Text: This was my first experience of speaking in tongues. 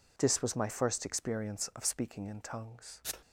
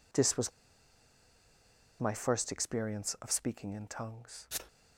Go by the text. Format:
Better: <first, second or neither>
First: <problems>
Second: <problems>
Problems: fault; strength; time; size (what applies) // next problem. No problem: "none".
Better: first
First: none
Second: pauses between "was" and "my"; strong; at 0.5 s; 1.4 s long